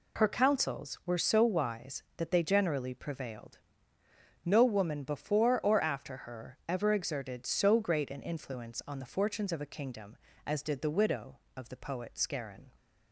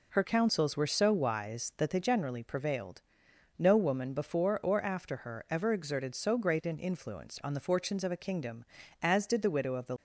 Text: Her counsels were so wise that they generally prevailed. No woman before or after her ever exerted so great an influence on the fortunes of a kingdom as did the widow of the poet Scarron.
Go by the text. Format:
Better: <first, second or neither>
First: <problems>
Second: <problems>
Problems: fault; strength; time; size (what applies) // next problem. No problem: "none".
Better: first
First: none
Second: stops before "poet Scarron"; at 9.9 s